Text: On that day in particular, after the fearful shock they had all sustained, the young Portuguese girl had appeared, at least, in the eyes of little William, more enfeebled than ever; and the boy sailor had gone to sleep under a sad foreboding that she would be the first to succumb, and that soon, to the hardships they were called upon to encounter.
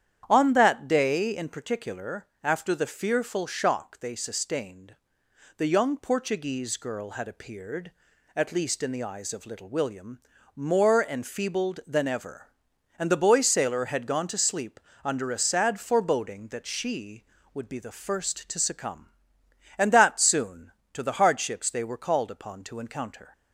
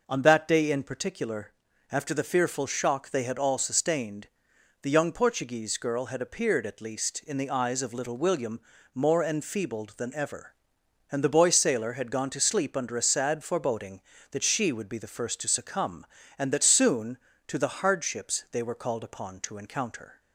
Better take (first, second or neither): second